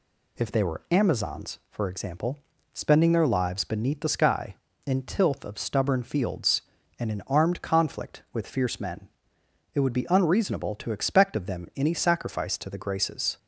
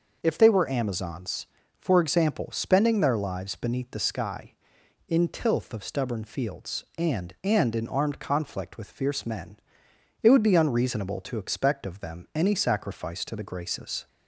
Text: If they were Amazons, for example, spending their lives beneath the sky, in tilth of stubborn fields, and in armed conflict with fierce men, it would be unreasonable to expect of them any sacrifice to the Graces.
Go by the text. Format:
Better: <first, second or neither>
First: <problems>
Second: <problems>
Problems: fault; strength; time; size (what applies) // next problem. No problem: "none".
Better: first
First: none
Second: says "and" twice; at 7.4 s